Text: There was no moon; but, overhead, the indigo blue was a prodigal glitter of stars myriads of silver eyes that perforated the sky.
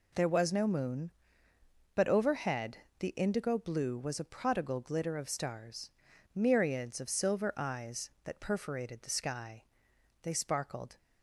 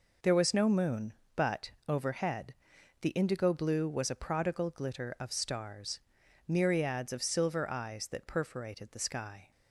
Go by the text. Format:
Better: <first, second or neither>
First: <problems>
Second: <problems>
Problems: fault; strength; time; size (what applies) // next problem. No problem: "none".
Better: second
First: pauses between "stars" and "myriads"; noticeable; at 5.8 s; 0.46 s long // goes on to say "They sparkled"; noticeable; from 10.2 s on; 0.76 s long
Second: pauses between "stars" and "myriads"; noticeable; at 6.0 s; 0.50 s long